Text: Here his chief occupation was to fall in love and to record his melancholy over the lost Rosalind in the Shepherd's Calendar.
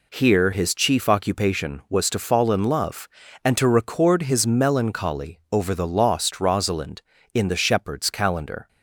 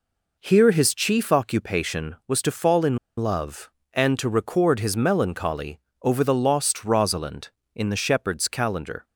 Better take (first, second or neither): first